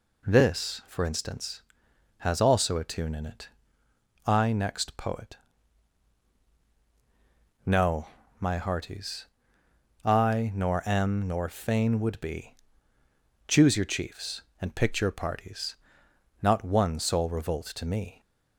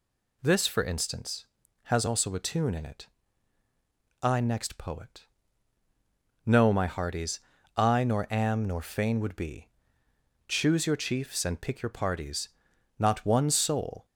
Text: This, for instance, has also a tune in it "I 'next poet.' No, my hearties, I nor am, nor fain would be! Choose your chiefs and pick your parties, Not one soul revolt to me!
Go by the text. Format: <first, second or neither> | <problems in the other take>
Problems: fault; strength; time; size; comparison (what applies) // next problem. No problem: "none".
first | pauses between "it" and "I"; at 3.0 s; 1.1 s long; noticeable in the first // stops before "revolt to me"; at 14.0 s